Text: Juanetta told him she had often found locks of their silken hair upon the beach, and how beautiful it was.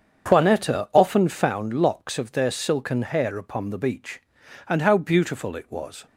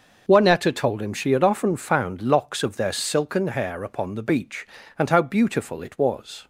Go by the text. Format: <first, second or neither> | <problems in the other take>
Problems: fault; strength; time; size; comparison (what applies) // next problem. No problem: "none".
second | starts louder than the rest; strong; until 1.3 s; 7.5 dB // skips "told him she had"; at 0.9 s